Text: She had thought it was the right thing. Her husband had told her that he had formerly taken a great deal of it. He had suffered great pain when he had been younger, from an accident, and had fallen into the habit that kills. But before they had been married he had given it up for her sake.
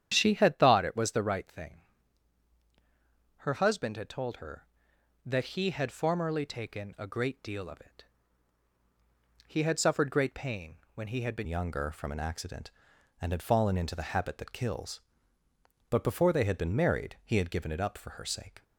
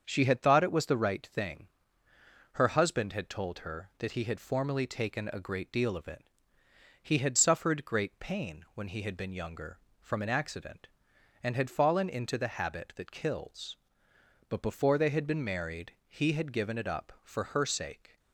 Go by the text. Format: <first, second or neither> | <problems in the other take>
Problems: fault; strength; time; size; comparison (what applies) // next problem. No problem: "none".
second | starts louder than the rest; strong; until 1.1 s; 9.5 dB; also in the second // pauses between "pain" and "when"; slight; at 10.7 s; 0.16 s long // changes voice at "younger"; from 11.4 s on; 7.2 s long